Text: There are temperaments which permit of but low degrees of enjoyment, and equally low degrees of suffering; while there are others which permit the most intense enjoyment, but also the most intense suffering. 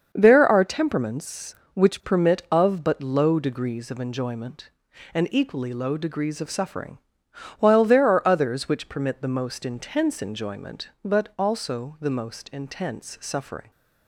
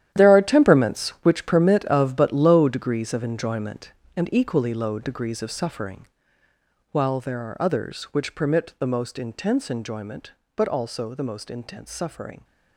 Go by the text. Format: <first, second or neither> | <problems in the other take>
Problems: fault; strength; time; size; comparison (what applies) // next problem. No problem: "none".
first | gets quieter; strong; throughout; 13 dB // starts louder than the rest; strong; until 1.1 s; 11.5 dB; also in the first